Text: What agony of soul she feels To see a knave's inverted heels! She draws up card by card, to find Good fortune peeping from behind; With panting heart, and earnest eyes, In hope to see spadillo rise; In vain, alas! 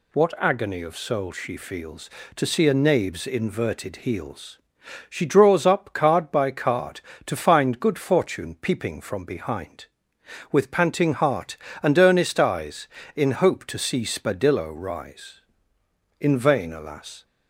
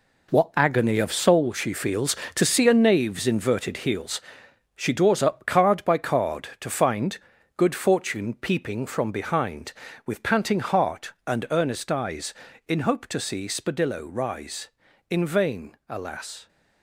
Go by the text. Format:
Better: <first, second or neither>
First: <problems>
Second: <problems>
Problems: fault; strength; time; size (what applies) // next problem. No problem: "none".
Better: first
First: none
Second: gets quieter; strong; throughout; 9.5 dB // pauses between "find" and "Good"; at 7.1 s; 0.38 s long